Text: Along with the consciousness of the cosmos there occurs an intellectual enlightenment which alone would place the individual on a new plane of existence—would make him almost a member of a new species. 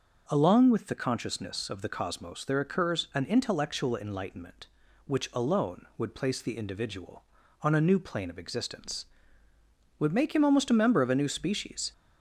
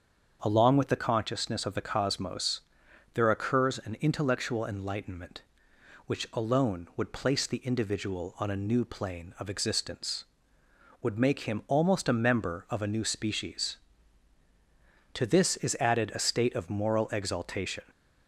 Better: first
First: none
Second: starts louder than the rest; until 1.4 s; 7 dB // pauses between "cosmos" and "there"; noticeable; at 2.6 s; 0.52 s long // goes on to say "To this is added a state of moral exaltation"; strong; from 15.1 s on; 2.7 s long

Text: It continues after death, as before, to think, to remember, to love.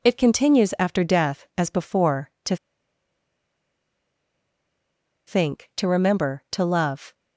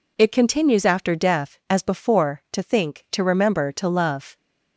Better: second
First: pauses between "to" and "think"; strong; at 2.5 s; 2.7 s long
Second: none

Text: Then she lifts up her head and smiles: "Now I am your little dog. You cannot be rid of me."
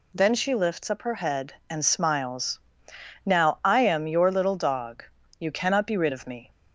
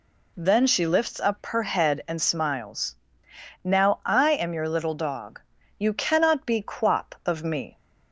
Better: first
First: none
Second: says "quap" for "rid"; at 6.6 s

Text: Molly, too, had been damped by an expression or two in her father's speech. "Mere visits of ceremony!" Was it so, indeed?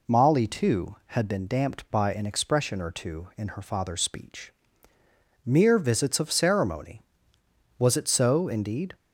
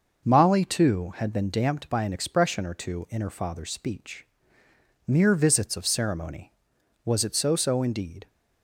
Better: first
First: none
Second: says "so" twice; at 7.5 s

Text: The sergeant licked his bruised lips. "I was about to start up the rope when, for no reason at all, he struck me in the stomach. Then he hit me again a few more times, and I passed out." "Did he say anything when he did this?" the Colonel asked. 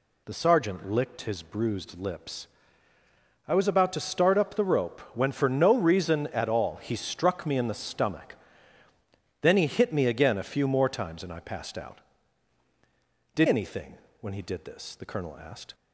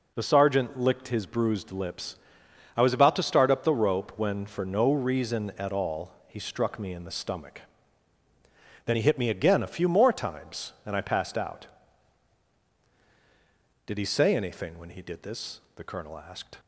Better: second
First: pauses between "rope" and "when"; slight; at 4.9 s; 0.16 s long // skips "he say"; at 13.4 s // pauses between "anything" and "when"; slight; at 13.9 s; 0.24 s long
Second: none

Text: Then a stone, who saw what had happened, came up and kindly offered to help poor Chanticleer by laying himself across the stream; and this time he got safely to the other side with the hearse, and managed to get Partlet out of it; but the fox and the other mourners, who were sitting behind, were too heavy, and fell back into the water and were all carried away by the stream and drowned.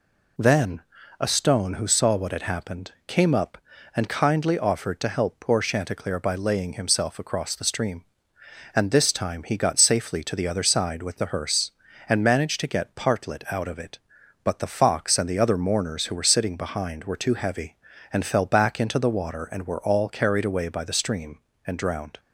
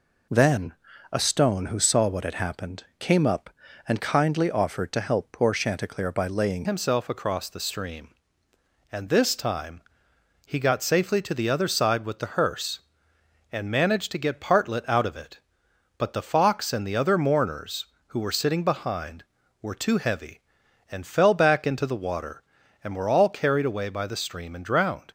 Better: first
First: pauses between "Then" and "a"; slight; at 0.8 s; 0.36 s long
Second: pauses between "Then" and "a"; slight; at 0.7 s; 0.36 s long // changes voice at "himself"; from 6.6 s on; 18.4 s long // pauses between "time" and "he"; noticeable; at 9.8 s; 0.64 s long

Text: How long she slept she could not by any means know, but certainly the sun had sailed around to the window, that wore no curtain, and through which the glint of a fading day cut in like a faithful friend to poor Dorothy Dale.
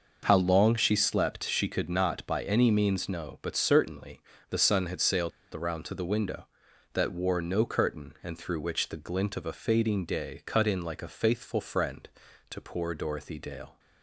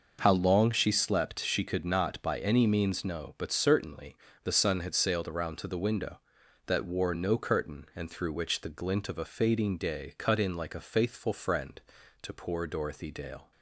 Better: second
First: pauses between "certainly" and "the"; slight; at 4.2 s; 0.26 s long // pauses between "sailed" and "around"; slight; at 5.3 s; 0.23 s long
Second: pauses between "certainly" and "the"; slight; at 4.1 s; 0.24 s long

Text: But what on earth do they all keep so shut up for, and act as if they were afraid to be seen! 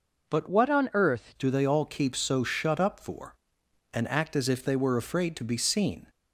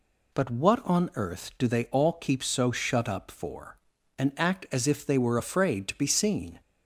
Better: second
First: changes voice from "what" to "earth"; from 0.4 to 1.3 s; 0.9 s long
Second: none

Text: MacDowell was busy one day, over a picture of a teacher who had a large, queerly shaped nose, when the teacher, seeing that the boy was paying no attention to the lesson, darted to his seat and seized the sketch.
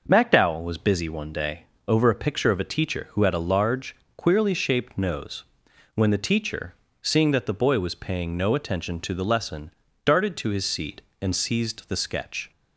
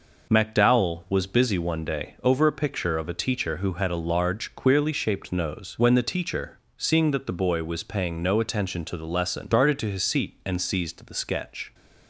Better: neither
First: none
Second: none

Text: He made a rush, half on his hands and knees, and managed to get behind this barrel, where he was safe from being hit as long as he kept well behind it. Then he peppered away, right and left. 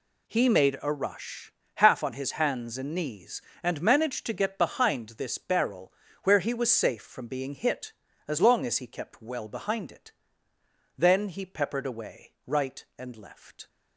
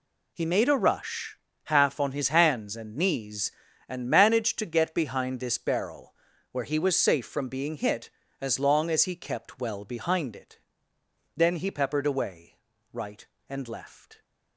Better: neither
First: none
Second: none

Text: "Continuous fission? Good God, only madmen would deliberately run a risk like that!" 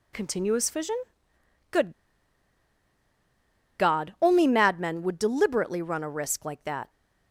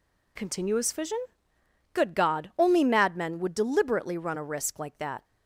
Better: second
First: pauses between "Good" and "God"; strong; at 1.9 s; 1.8 s long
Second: none

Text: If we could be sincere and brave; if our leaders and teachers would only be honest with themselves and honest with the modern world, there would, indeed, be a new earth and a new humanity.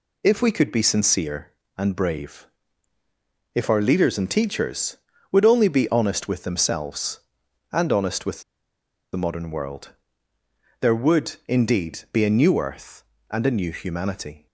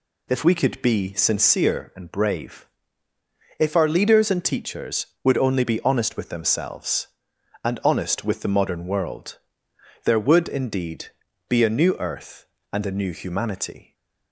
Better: second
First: pauses between "with" and "the"; noticeable; at 8.4 s; 0.72 s long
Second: none

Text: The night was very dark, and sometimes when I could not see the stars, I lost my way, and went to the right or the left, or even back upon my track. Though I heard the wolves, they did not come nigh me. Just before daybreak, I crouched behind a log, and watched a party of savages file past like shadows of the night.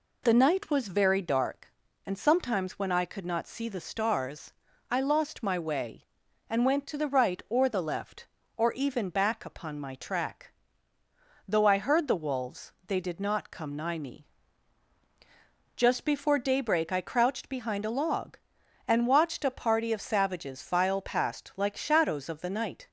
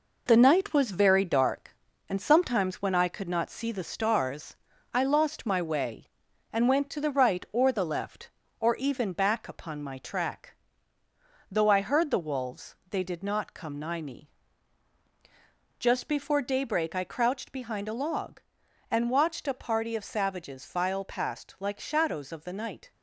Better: first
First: none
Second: gets quieter; noticeable; throughout; 5.5 dB

